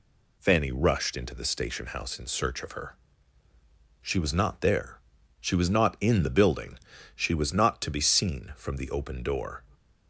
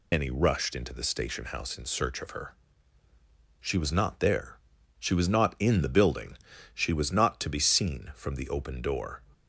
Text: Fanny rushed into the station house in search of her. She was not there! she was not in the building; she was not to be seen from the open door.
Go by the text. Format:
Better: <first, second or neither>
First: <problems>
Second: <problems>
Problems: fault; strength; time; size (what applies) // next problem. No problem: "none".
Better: first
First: none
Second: loses the start of "Fanny"; at 0.1 s; 150 ms